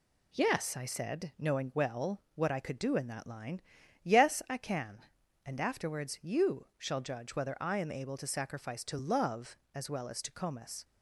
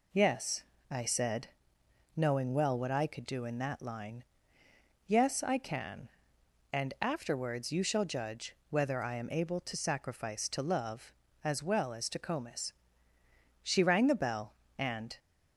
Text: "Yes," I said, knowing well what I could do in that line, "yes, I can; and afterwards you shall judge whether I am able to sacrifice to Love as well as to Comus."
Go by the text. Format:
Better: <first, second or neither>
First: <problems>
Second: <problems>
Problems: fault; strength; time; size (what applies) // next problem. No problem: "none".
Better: first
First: none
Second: pauses between "judge" and "whether"; slight; at 8.5 s; 0.16 s long // goes on to say "She rang the bell and"; from 13.6 s on; 1.5 s long